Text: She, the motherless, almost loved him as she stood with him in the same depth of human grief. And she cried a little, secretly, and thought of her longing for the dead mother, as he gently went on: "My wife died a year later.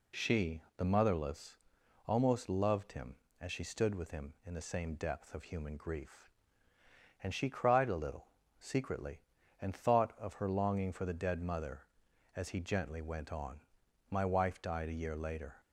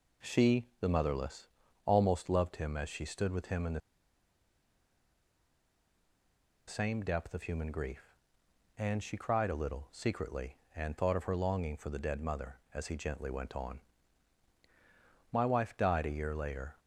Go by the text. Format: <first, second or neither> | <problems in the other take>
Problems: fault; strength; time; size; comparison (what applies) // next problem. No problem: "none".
first | pauses between "the" and "same"; strong; at 3.7 s; 2.8 s long